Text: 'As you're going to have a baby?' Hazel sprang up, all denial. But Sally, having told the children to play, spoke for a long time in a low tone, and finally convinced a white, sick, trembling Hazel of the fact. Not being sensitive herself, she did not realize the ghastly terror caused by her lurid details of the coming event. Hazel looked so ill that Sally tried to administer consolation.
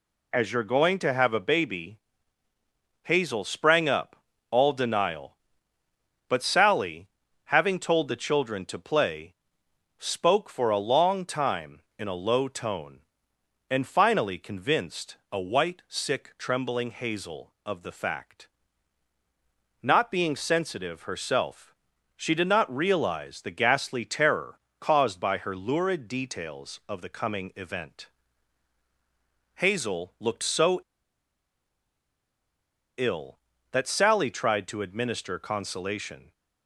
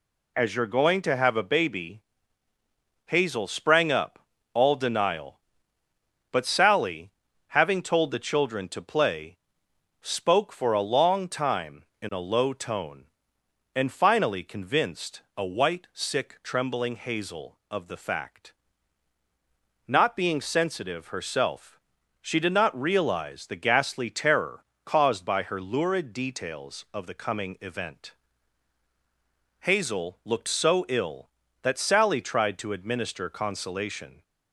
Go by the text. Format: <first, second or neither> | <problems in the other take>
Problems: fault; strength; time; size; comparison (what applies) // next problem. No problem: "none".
second | pauses between "convinced" and "a"; slight; at 15.1 s; 0.16 s long; slight in the second // pauses between "terror" and "caused"; slight; at 24.5 s; 0.20 s long; slight in the second // pauses between "so" and "ill"; strong; at 30.7 s; 2.1 s long